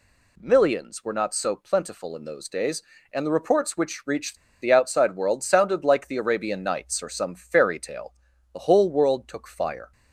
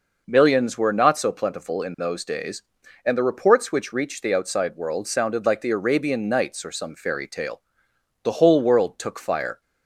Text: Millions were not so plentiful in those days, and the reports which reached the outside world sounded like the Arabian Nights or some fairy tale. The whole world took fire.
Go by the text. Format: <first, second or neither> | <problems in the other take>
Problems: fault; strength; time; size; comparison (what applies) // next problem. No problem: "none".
second | pauses between "reached" and "the"; slight; at 4.3 s; 0.26 s long